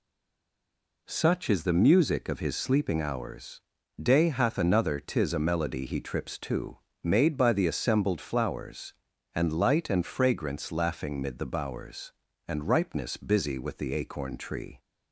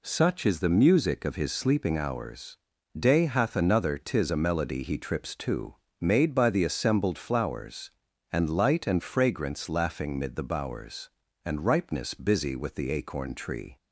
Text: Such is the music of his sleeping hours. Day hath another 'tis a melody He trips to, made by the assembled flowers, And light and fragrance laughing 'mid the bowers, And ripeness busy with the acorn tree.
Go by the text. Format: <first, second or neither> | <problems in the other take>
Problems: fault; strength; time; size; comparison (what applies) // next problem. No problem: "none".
second | stays silent before the first word; until 1.0 s; 1.0 s long